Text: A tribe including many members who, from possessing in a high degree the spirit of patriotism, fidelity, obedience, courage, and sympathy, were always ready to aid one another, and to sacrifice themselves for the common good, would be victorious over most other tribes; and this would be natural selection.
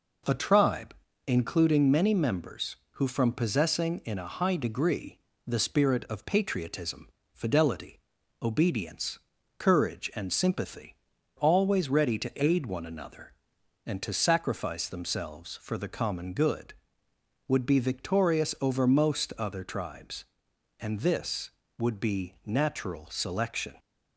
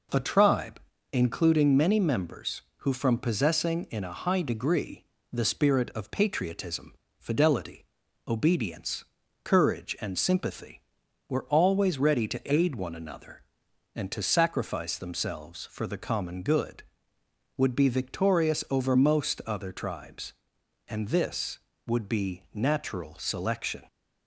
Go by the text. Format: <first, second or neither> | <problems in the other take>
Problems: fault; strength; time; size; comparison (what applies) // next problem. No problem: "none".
second | pauses between "tribe" and "including"; slight; at 0.9 s; 0.32 s long; slight in the second // pauses between "degree" and "the"; slight; at 5.1 s; 0.28 s long; slight in the second // skips "were"; at 11.1 s